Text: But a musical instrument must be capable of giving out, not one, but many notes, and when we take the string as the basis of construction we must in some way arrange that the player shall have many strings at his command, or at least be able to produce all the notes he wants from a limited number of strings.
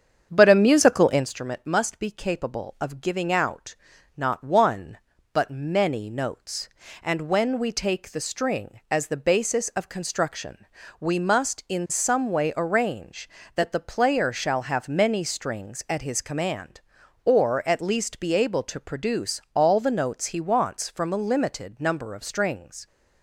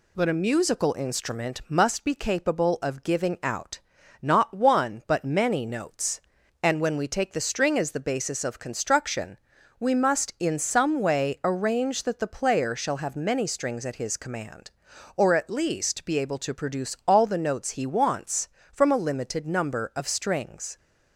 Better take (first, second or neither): second